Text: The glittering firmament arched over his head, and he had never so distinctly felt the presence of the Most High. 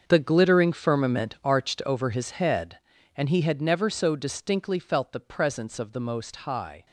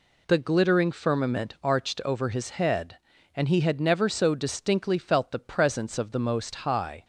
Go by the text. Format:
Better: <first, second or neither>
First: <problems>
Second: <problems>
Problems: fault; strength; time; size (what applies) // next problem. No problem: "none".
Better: second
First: gets quieter; strong; throughout; 13.5 dB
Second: none